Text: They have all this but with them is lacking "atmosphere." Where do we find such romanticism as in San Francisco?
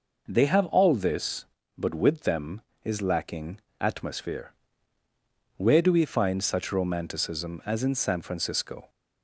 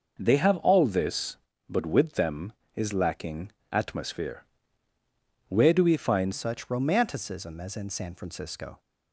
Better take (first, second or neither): first